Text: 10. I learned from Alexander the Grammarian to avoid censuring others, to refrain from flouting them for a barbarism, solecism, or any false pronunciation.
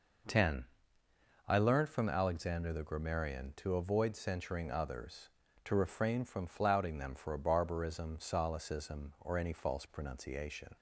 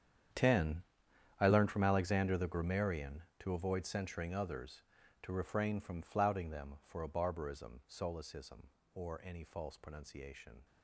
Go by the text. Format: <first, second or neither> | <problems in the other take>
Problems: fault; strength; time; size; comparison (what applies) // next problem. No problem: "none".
first | gets quieter; strong; throughout; 17 dB